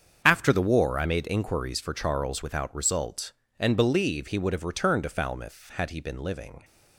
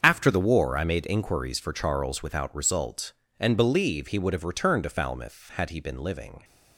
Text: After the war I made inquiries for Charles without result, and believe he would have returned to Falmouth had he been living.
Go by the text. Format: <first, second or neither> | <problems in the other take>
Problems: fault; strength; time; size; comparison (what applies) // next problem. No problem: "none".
neither | starts louder than the rest; strong; the same in both